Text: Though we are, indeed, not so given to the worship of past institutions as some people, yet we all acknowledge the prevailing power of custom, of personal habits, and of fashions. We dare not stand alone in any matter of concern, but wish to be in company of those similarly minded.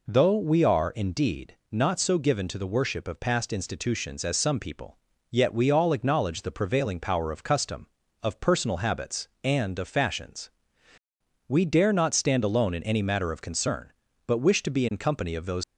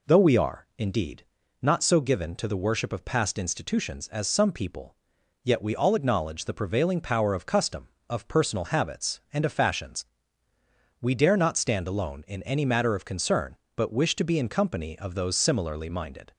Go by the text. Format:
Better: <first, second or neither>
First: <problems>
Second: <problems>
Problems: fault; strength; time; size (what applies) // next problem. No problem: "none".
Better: second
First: stops before "similarly minded"; at 15.6 s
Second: none